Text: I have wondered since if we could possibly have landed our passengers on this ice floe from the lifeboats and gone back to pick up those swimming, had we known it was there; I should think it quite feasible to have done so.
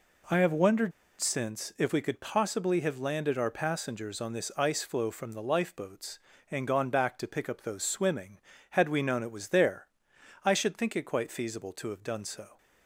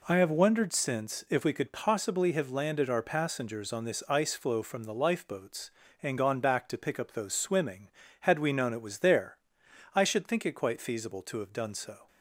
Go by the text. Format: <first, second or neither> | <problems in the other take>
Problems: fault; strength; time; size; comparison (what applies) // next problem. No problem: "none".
second | pauses between "wondered" and "since"; slight; at 0.9 s; 0.29 s long